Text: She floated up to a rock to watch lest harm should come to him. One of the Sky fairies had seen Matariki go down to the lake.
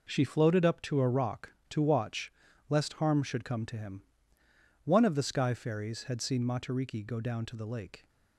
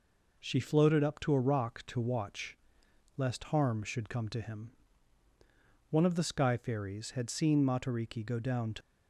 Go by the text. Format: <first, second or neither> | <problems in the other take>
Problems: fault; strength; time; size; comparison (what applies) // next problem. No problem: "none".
first | pauses between "watch" and "lest"; noticeable; at 2.5 s; 0.60 s long; also in the first // stops before "the lake"; at 8.8 s